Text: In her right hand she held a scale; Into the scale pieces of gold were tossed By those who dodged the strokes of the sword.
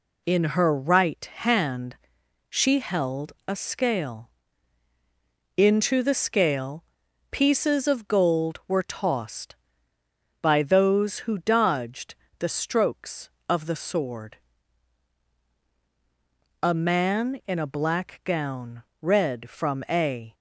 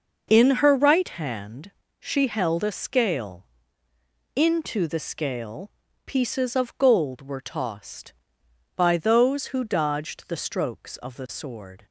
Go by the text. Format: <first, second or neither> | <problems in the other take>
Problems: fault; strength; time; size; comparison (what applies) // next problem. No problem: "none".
second | pauses between "hand" and "she"; noticeable; at 1.9 s; 0.54 s long; slight in the second // pauses between "scale" and "pieces"; at 6.8 s; 0.44 s long; slight in the second // pauses between "dodged" and "the"; slight; at 12.1 s; 0.24 s long // goes on to say "A man in a black gown read from a"; strong; from 16.5 s on; 3.7 s long